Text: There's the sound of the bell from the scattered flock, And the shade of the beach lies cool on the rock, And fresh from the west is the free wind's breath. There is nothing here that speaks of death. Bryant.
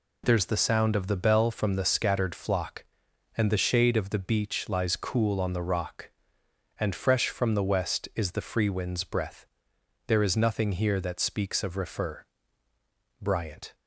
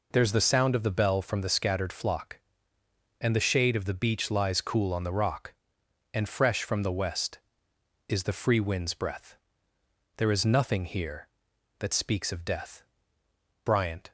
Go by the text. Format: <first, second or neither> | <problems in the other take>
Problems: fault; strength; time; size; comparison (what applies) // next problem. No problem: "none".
second | says "refer" for "death"; at 11.7 s